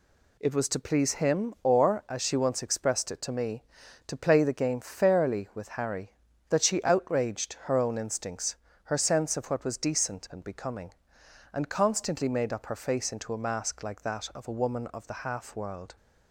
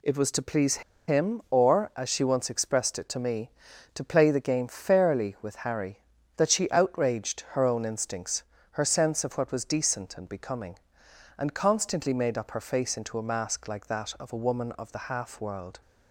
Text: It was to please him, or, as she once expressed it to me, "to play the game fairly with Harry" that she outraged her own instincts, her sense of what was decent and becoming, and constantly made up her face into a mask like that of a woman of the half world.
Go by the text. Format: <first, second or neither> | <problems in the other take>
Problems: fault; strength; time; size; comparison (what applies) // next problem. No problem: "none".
first | pauses between "please" and "him"; slight; at 0.8 s; 0.27 s long